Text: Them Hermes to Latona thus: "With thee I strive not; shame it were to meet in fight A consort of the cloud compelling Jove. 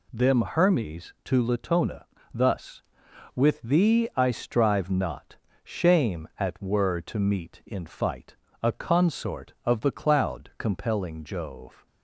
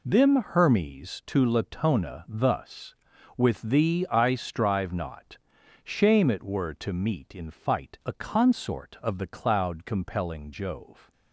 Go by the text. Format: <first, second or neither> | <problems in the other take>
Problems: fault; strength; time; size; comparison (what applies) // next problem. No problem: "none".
second | pauses between "Latona" and "thus"; slight; at 2.0 s; 0.28 s long // says "at" for "it"; at 6.3 s // pauses between "fight" and "A"; slight; at 8.3 s; 0.26 s long